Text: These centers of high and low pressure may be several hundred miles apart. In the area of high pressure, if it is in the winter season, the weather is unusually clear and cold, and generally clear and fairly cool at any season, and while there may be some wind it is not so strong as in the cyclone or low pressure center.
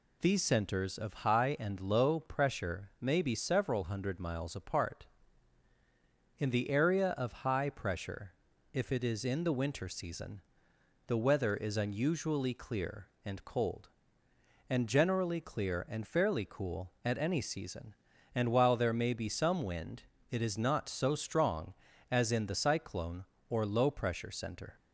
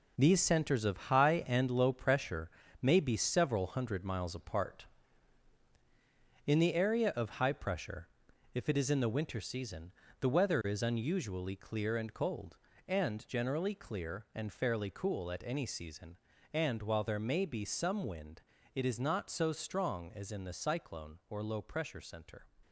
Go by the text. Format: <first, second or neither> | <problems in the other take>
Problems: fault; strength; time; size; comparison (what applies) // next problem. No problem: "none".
first | gets quieter; strong; throughout; 8.5 dB // pauses between "pressure" and "may"; slight; at 2.4 s; 0.32 s long // pauses between "wind" and "it"; slight; at 18.4 s; 0.34 s long; slight in the first